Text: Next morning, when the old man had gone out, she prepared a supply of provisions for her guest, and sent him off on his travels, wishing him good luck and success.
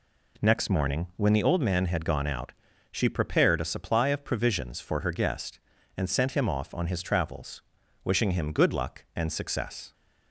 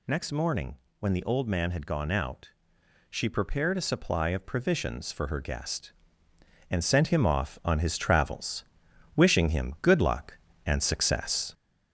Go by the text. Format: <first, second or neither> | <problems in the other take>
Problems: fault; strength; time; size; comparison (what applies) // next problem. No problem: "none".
first | gets louder; noticeable; throughout; 4.5 dB